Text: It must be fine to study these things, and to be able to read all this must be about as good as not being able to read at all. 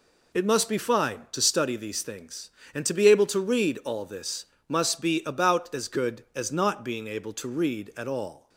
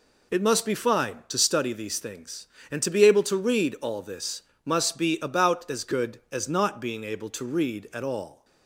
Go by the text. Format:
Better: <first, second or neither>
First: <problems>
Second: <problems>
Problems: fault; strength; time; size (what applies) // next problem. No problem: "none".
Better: neither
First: pauses between "this" and "must"; slight; at 4.4 s; 0.22 s long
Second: pauses between "this" and "must"; slight; at 4.4 s; 0.22 s long